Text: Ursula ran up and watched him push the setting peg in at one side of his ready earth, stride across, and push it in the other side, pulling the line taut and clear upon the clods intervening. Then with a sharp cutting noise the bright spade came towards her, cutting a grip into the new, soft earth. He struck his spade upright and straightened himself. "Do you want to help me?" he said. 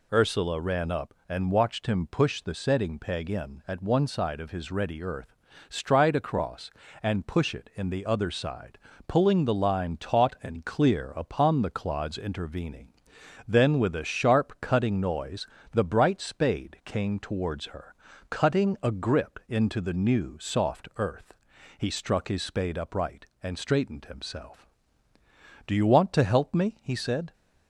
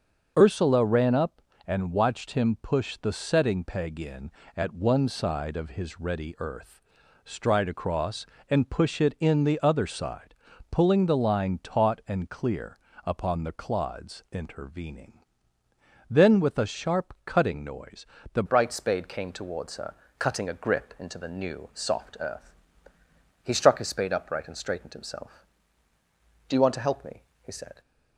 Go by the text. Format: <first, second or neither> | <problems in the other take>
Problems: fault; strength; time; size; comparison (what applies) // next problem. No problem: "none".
first | starts louder than the rest; noticeable; until 1.3 s; 6 dB // pauses between "clear" and "upon"; slight; at 12.7 s; 0.26 s long // pauses between "noise" and "the"; slight; at 18.0 s; 0.26 s long; slight in the first // changes voice at "bright"; from 18.4 s on; 9.4 s long